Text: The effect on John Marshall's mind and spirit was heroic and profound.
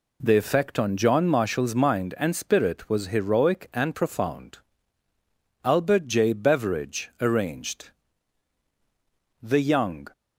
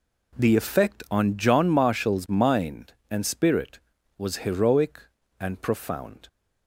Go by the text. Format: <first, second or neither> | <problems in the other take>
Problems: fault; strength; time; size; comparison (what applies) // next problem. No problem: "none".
second | goes on to say "Albert J Beveridge Arranged THE YOUNG"; strong; from 5.6 s on; 4.4 s long